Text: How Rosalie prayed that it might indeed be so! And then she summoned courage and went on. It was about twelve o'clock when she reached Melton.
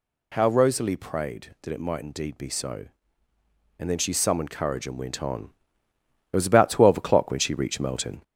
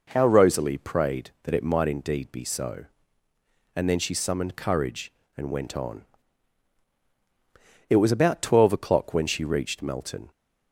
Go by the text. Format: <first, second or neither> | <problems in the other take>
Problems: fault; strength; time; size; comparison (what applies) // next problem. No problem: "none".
second | gets louder; slight; throughout; 3 dB